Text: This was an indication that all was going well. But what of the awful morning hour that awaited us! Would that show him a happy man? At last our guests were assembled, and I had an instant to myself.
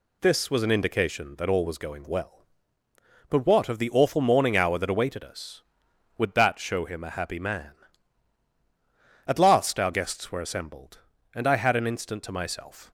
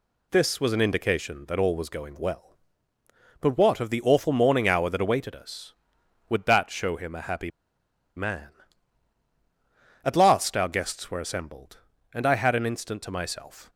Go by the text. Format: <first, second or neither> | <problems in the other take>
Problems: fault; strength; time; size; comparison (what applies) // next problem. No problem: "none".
first | pauses between "happy" and "man"; noticeable; at 7.4 s; 0.66 s long